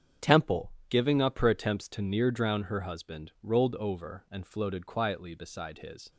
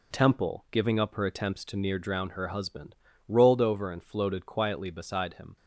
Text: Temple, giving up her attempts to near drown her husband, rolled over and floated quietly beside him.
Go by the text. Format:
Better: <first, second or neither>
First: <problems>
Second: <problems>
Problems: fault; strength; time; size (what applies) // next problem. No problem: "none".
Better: second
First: starts louder than the rest; strong; until 1.4 s; 8 dB // says "his" for "him"; at 5.7 s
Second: none